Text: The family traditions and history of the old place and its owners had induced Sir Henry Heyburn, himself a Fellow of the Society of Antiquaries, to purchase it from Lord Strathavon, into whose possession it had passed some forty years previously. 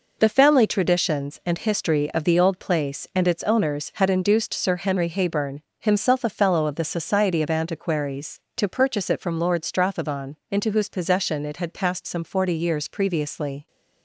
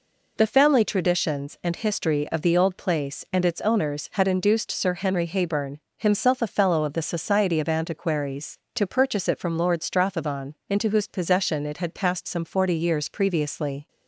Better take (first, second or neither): second